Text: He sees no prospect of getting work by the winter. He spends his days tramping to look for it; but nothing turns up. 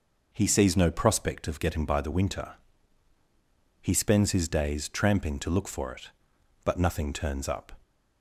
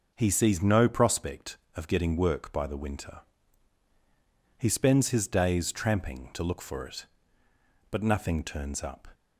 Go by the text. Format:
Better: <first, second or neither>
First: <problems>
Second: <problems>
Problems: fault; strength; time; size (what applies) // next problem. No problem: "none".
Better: second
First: skips "work"; at 1.8 s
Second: none